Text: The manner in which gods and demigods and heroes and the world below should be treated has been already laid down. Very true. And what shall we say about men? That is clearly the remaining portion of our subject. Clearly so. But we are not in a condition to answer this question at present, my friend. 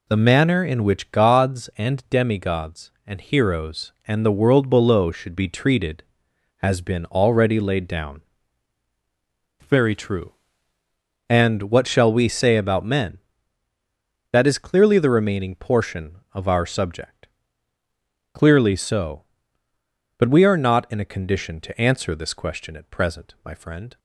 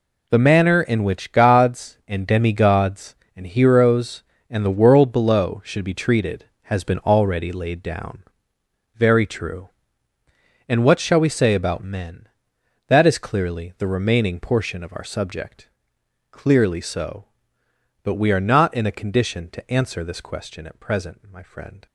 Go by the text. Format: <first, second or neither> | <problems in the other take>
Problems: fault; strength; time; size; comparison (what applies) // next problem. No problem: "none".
neither | none